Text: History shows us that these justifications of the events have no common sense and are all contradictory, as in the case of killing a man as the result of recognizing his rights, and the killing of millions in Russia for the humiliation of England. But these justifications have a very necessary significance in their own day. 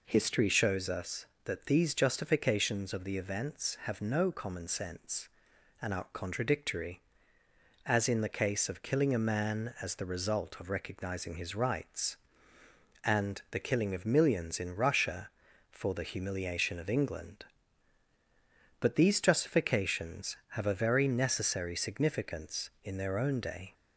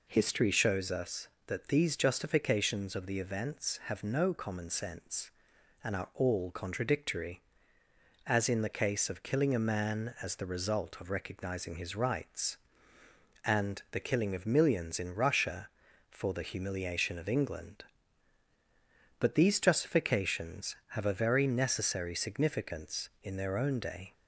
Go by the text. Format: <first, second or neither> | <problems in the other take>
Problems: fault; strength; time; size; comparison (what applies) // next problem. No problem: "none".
second | skips "all"; at 6.0 s